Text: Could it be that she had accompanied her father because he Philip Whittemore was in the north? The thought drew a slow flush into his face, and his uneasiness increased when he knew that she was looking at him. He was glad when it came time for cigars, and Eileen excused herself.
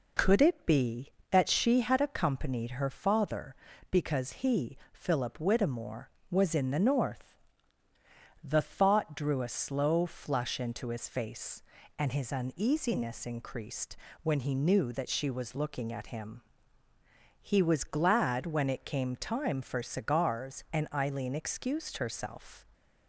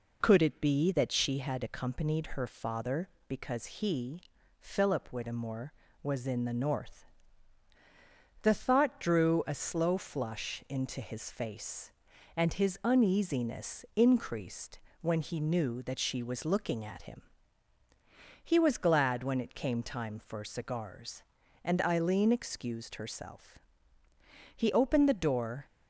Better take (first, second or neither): first